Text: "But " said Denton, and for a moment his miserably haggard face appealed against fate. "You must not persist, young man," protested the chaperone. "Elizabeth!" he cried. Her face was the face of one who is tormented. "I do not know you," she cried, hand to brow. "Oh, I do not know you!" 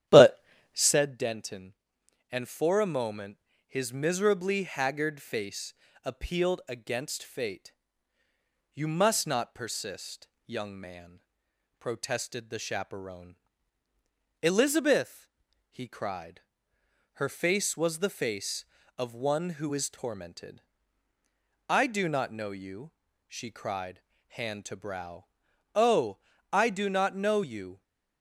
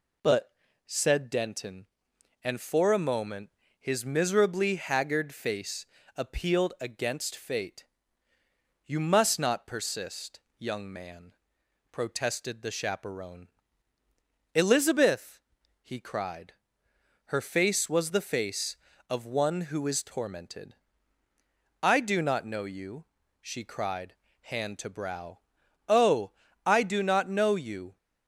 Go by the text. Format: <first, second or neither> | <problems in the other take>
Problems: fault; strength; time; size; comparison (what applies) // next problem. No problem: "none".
second | starts louder than the rest; strong; until 1.0 s; 11 dB // pauses between "moment" and "his"; slight; at 3.3 s; 0.28 s long; slight in the second // pauses between "face" and "appealed"; slight; at 5.7 s; 0.30 s long; slight in the second